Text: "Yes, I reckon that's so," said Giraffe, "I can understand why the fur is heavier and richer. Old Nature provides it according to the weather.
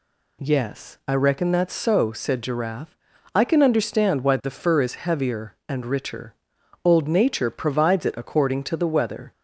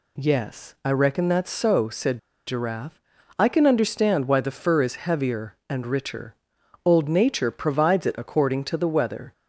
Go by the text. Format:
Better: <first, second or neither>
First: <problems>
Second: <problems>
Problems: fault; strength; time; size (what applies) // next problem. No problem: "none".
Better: first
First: none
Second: pauses between "said" and "Giraffe"; slight; at 2.1 s; 0.28 s long